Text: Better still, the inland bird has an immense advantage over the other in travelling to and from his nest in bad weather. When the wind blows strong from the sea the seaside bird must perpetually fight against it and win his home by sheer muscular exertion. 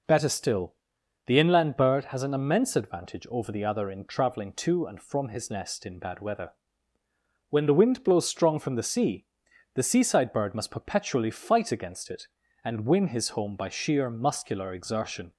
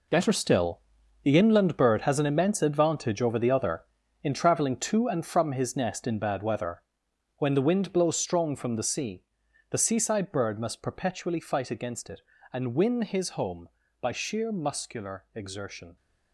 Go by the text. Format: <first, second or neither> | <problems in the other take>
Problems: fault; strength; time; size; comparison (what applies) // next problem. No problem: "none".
first | gets quieter; strong; throughout; 11.5 dB // pauses between "sea" and "the"; noticeable; at 9.2 s; 0.48 s long; noticeable in the first